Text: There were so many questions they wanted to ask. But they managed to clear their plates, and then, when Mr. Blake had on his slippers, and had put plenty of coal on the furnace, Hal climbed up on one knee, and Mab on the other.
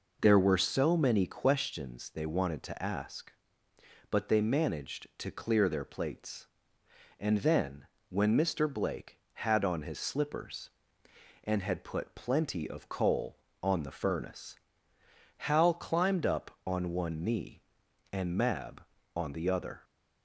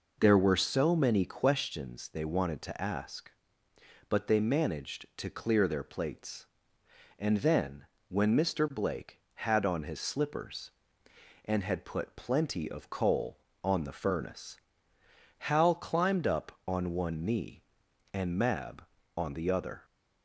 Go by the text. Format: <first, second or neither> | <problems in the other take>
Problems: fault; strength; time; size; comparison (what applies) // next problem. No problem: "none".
neither | none